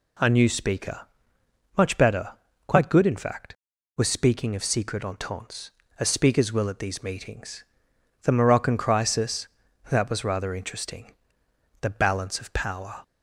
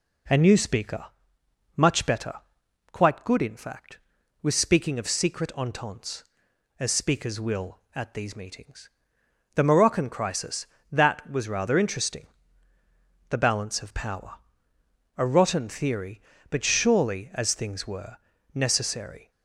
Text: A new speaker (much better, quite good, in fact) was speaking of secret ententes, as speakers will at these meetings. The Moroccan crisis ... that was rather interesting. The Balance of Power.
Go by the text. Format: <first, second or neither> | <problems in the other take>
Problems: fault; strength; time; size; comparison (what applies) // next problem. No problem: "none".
first | goes on to say "A rotten theory but surely as things were necessary"; strong; from 15.1 s on; 4.1 s long